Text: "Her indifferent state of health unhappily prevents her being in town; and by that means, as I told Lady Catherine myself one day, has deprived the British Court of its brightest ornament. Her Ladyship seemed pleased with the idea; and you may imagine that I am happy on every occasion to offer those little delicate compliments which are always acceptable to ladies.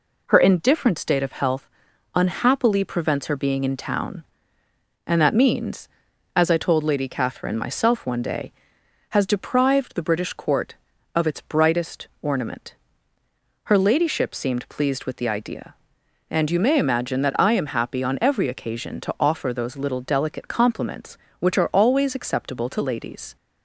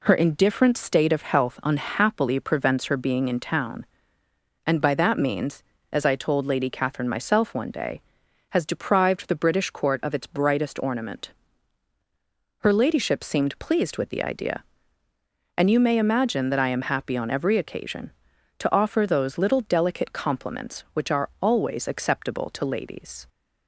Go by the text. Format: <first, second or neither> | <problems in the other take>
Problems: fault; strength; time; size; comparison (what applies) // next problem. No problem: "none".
second | pauses between "health" and "unhappily"; noticeable; at 1.6 s; 0.48 s long // skips "by"; at 5.2 s